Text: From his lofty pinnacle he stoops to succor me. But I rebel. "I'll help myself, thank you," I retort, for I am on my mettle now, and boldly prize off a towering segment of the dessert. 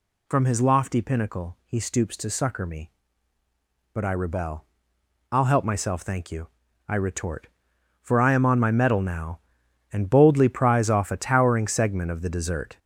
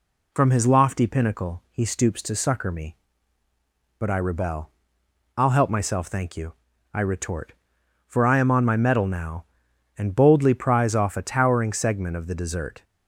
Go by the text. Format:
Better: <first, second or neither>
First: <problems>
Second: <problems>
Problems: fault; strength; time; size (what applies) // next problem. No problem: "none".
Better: second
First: gets louder; noticeable; throughout; 6 dB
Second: none